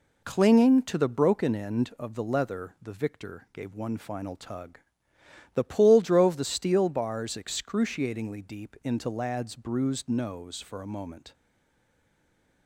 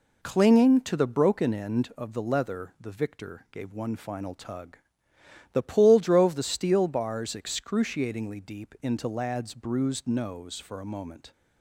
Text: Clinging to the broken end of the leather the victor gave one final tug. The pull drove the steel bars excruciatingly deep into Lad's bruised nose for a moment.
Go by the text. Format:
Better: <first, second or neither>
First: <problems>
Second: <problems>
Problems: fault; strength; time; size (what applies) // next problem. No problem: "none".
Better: second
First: stays silent after the last word; noticeable; from 11.3 s on; 1.3 s long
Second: none